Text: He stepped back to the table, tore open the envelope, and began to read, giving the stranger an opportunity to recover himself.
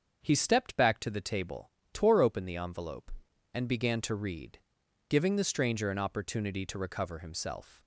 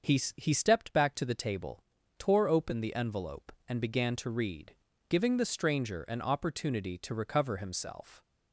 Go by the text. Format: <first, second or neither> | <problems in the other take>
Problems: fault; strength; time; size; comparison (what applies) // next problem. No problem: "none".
first | starts louder than the rest; until 1.2 s; 6 dB; also in the first // says "He" twice; at 0.3 s